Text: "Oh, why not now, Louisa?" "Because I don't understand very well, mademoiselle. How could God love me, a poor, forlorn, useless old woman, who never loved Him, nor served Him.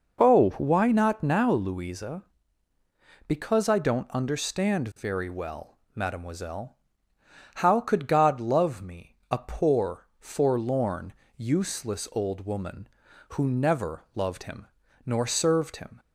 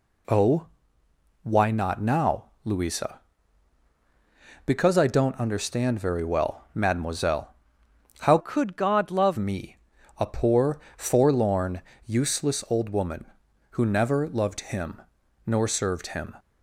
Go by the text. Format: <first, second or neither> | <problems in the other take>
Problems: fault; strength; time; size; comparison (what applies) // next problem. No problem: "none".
first | changes voice from "could" to "love"; from 8.3 to 9.3 s; 1.0 s long